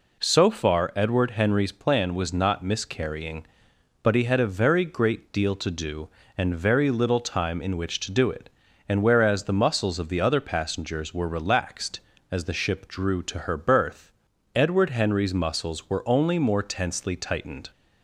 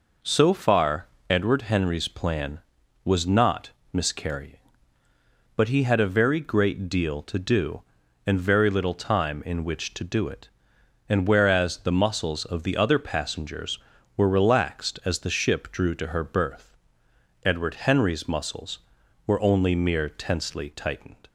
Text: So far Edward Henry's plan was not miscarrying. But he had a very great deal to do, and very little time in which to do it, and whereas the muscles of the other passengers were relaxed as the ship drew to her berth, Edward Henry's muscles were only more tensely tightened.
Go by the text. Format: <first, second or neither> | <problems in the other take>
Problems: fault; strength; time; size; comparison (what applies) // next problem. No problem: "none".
first | pauses between "far" and "Edward"; slight; at 1.0 s; 0.24 s long // pauses between "not" and "miscarrying"; slight; at 3.7 s; 0.20 s long // says "mere" for "more"; at 19.7 s